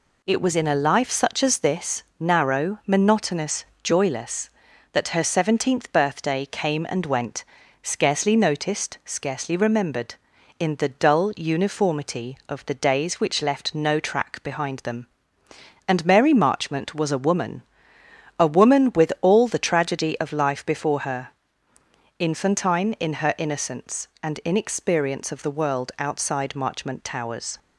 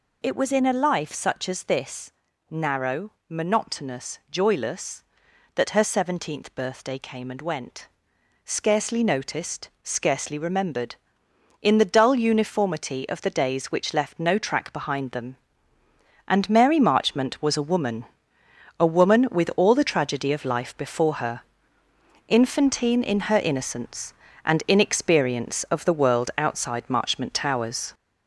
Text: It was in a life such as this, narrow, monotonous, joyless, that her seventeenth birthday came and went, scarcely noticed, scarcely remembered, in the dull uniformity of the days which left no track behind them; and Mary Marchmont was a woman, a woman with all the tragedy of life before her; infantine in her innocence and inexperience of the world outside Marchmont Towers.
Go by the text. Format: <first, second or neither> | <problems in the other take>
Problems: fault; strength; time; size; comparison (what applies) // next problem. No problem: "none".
first | gets louder; noticeable; throughout; 5 dB